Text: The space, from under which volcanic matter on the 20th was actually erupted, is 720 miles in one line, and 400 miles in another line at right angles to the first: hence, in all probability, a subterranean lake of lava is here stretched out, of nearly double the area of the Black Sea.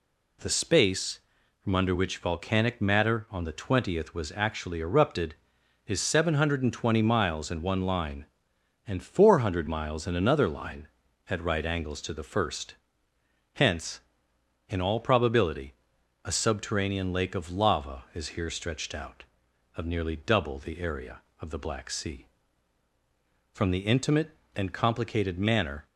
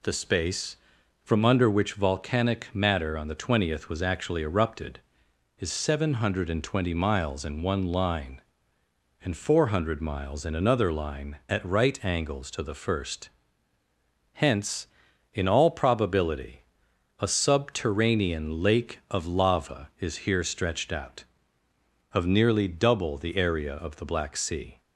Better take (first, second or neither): second